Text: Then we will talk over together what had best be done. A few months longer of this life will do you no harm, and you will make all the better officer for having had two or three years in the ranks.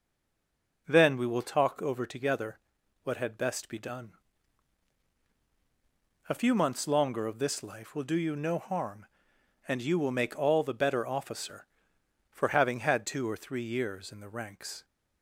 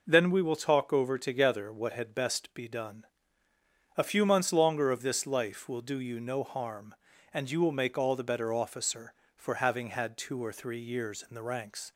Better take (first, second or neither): second